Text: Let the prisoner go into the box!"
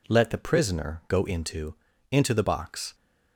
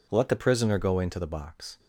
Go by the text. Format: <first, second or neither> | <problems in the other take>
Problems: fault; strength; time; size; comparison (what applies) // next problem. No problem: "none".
second | says "into" twice; at 2.1 s